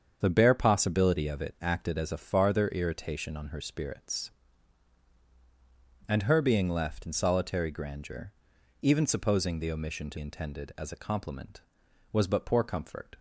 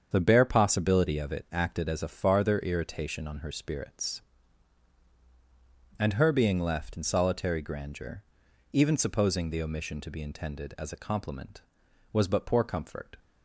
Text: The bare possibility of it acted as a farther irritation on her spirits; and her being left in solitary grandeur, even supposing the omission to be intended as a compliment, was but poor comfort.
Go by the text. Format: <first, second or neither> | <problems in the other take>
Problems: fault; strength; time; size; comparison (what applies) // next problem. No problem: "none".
second | starts louder than the rest; strong; until 1.2 s; 7.5 dB; strong in the second // skips "be"; at 10.1 s